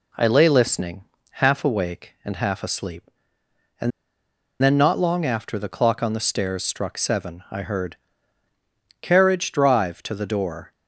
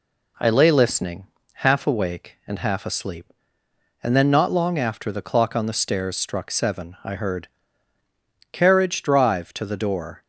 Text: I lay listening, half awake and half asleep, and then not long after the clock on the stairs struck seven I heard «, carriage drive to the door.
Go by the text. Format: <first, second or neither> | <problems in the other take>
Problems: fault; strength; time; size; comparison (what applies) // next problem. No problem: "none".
second | pauses between "and" and "then"; noticeable; at 3.9 s; 0.71 s long